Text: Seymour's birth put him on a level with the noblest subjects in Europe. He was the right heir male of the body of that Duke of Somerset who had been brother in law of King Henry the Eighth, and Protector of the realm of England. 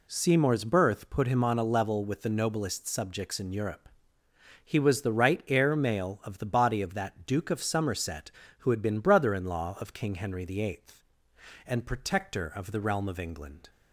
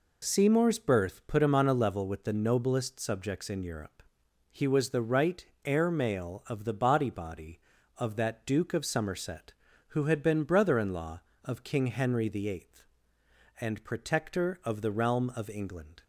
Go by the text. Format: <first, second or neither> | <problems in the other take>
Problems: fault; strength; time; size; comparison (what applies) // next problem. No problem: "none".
first | pauses between "right" and "heir"; slight; at 5.4 s; 0.20 s long // says "body" twice; at 7.0 s